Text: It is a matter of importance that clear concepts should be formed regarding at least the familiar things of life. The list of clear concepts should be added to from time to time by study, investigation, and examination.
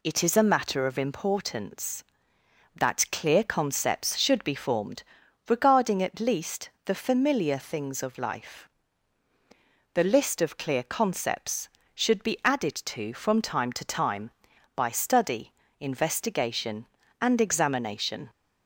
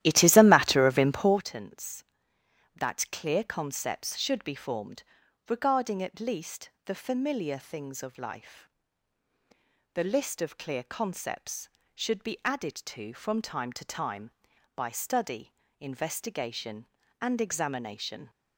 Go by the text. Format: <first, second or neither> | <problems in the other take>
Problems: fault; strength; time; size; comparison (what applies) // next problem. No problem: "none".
first | starts louder than the rest; strong; until 1.5 s; 13 dB // pauses between "formed" and "regarding"; noticeable; at 5.0 s; 0.46 s long; noticeable in the first // pauses between "least" and "the"; slight; at 6.6 s; 0.16 s long; slight in the first